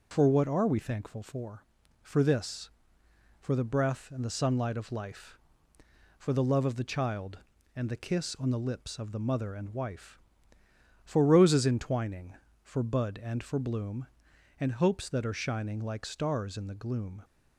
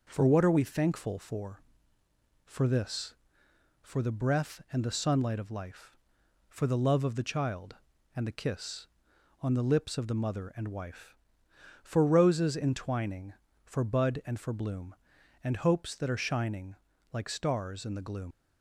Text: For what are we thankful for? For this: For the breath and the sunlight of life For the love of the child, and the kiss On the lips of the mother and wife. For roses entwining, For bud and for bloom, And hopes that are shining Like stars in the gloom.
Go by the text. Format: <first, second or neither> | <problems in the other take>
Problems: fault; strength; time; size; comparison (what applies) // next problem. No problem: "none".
first | pauses between "shining" and "Like"; slight; at 16.7 s; 0.36 s long // leaves "gloom" unfinished; at 18.3 s; 90 ms